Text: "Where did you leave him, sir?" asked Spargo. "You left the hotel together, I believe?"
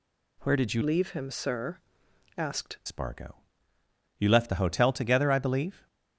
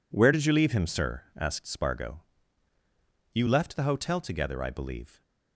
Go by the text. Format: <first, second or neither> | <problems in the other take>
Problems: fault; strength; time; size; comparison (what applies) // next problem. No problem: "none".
second | changes voice from "leave" to "asked"; from 0.8 to 2.7 s; 1.9 s long